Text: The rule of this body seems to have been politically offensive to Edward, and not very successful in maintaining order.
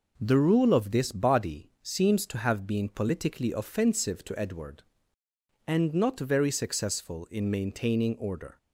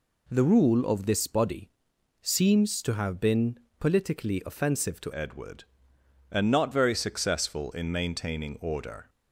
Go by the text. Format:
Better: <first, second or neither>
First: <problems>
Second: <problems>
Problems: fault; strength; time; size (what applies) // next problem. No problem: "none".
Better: first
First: none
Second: pauses between "body" and "seems"; noticeable; at 1.7 s; 0.50 s long // pauses between "been" and "politically"; slight; at 3.5 s; 0.20 s long // changes voice at "Edward"; from 5.1 s on; 3.9 s long